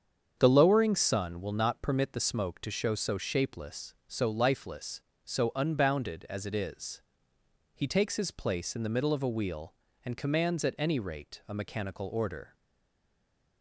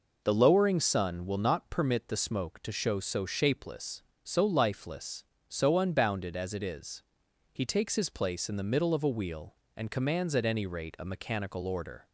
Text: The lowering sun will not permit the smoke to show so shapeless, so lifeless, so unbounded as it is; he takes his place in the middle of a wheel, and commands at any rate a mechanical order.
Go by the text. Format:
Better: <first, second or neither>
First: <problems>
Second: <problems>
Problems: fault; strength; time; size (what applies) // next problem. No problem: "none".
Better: second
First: starts louder than the rest; strong; until 1.4 s; 7.5 dB // stays silent after the last word; from 12.5 s on; 1.1 s long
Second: none